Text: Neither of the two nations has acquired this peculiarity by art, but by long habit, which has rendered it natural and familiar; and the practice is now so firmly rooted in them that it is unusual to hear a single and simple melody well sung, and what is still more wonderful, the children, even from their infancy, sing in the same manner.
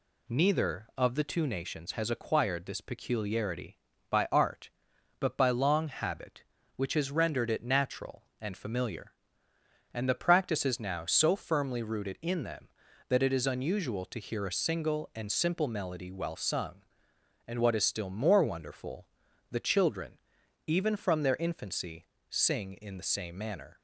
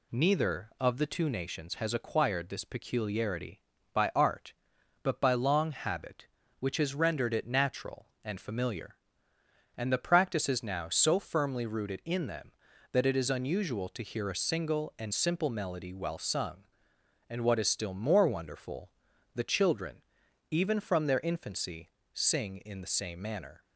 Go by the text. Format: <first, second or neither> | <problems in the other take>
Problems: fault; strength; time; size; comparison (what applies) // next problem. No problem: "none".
neither | none